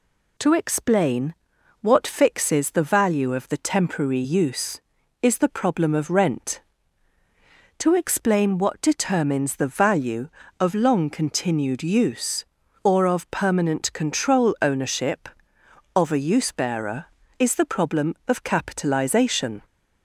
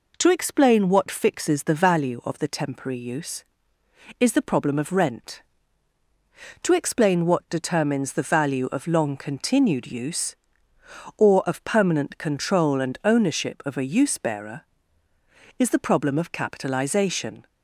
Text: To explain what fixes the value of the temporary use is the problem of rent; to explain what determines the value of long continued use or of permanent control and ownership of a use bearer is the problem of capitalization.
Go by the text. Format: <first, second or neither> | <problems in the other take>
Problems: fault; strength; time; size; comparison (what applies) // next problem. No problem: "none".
second | pauses between "explain" and "what"; noticeable; at 1.3 s; 0.48 s long // skips "and"; at 14.5 s